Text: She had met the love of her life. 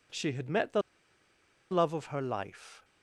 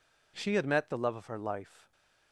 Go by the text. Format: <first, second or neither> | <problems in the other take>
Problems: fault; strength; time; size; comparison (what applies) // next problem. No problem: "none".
second | pauses between "the" and "love"; noticeable; at 0.8 s; 0.90 s long